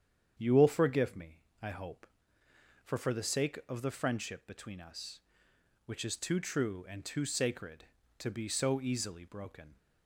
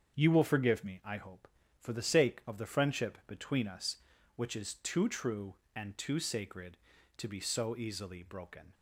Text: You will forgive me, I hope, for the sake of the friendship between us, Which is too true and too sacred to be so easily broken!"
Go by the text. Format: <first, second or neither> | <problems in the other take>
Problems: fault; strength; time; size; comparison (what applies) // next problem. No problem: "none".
second | starts louder than the rest; strong; until 1.3 s; 8.5 dB; strong in the second // says "for" twice; at 2.9 s